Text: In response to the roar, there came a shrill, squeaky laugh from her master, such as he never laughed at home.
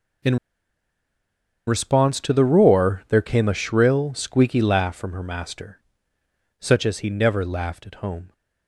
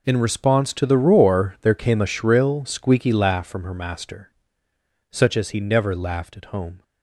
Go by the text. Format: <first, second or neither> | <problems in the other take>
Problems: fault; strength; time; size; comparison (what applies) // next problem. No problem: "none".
second | pauses between "In" and "response"; strong; at 0.3 s; 1.3 s long